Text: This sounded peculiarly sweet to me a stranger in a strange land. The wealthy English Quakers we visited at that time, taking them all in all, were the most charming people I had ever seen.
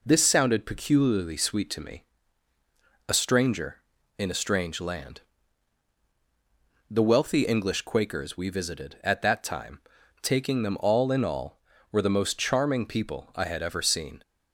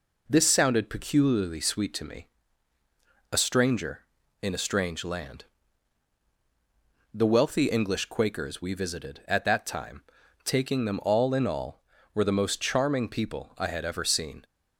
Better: neither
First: pauses between "me" and "a"; at 2.0 s; 1.0 s long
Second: pauses between "me" and "a"; at 2.2 s; 1.0 s long

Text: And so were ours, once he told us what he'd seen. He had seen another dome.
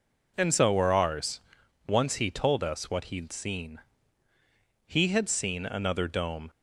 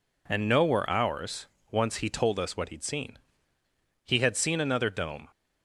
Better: first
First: none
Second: says "no" for "so"; at 0.4 s

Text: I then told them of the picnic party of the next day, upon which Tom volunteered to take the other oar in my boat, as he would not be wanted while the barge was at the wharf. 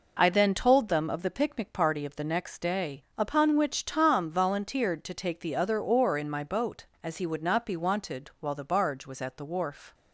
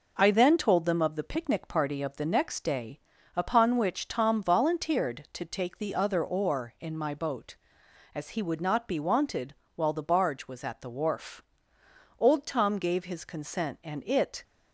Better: first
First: none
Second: pauses between "wanted" and "while"; slight; at 9.5 s; 0.22 s long // goes on to say "Old Tom gave his consent and it"; strong; from 12.1 s on; 2.2 s long

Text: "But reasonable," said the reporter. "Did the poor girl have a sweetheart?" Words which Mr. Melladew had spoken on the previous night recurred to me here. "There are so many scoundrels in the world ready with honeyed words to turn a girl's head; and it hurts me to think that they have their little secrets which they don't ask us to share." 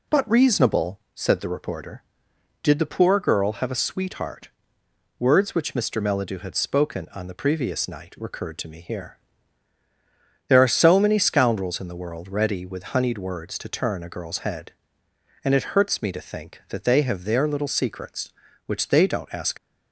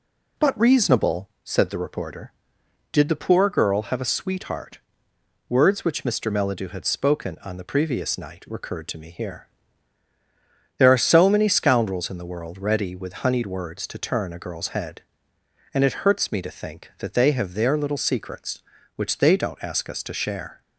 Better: second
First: stops before "us to share"; at 19.5 s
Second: none

